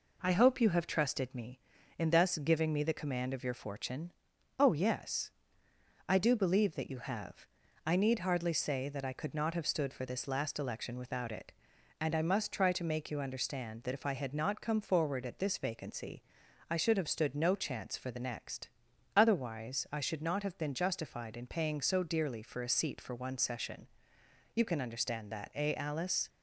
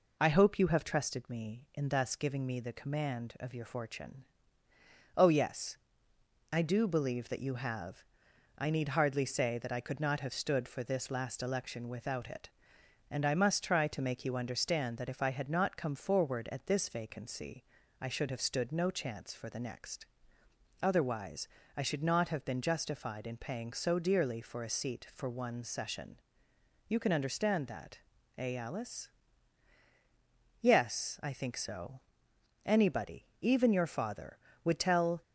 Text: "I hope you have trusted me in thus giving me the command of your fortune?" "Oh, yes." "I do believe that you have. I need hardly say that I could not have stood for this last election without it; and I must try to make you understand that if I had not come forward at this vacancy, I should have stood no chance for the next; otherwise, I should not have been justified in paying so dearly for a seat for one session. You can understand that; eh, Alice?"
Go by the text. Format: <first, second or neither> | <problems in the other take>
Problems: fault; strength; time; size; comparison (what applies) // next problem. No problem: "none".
first | goes on to say "Yes I think so Anybody even your father would tell"; strong; from 30.5 s on; 4.6 s long